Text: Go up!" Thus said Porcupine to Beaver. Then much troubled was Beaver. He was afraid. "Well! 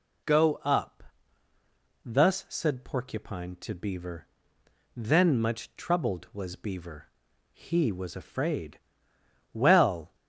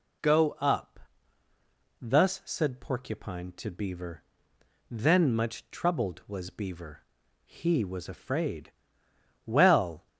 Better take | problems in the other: neither | none

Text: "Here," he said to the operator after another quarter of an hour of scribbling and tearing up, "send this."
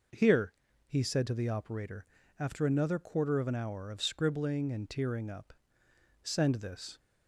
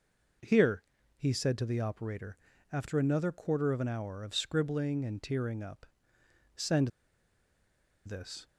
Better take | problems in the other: first | pauses between "operator" and "after"; slight; at 2.3 s; 0.34 s long; slight in the first // pauses between "send" and "this"; at 6.8 s; 1.1 s long

